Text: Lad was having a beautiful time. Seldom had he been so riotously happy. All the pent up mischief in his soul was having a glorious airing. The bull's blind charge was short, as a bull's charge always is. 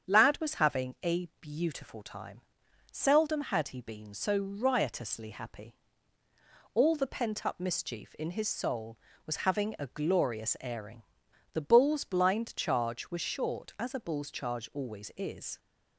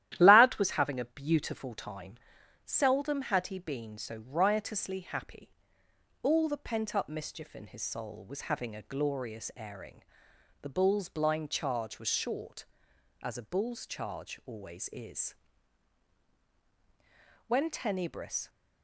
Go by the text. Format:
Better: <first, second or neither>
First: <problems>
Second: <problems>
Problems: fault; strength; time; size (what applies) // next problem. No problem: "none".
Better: first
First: starts louder than the rest; strong; until 1.1 s; 8 dB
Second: starts louder than the rest; strong; until 1.2 s; 12.5 dB // goes on to say "When Tenebris"; noticeable; from 17.4 s on; 1.0 s long